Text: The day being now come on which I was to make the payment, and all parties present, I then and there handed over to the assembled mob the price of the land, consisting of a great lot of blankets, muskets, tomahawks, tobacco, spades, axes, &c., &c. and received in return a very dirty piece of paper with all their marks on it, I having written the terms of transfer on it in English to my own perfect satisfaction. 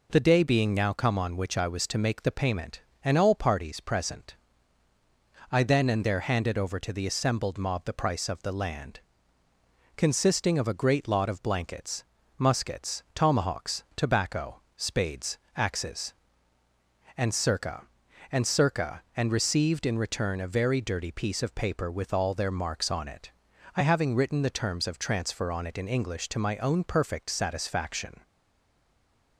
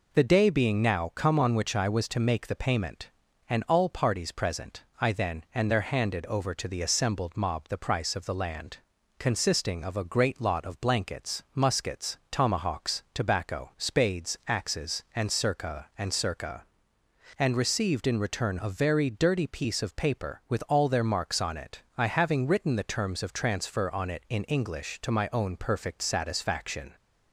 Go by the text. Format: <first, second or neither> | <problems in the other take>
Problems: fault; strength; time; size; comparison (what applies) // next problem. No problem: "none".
second | stays silent after the last word; noticeable; from 28.2 s on; 1.1 s long